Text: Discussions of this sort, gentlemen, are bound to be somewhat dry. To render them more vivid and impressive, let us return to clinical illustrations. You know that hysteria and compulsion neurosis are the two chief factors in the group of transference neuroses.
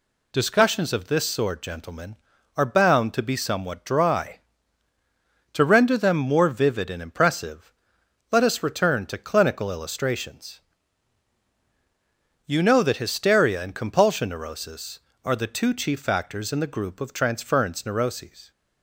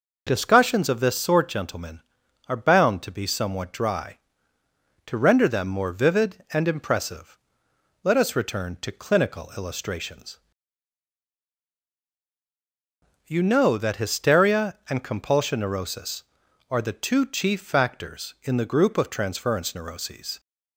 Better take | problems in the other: neither | none

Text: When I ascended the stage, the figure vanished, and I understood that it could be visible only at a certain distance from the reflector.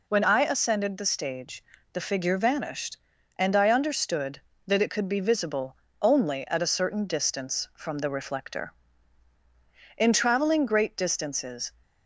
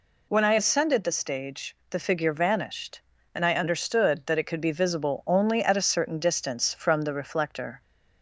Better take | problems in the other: second | pauses between "visible" and "only"; slight; at 5.7 s; 0.24 s long // goes on to say "In traveling great distances"; strong; from 9.9 s on; 1.7 s long

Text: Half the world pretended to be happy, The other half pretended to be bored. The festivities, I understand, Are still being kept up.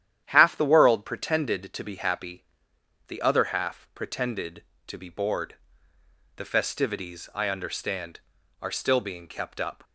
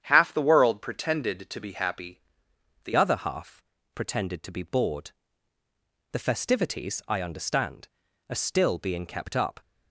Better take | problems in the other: first | starts louder than the rest; strong; until 1.0 s; 9 dB; strong in the first // changes voice at "other"; from 2.9 s on; 6.6 s long // pauses between "half" and "pretended"; slight; at 3.6 s; 0.34 s long

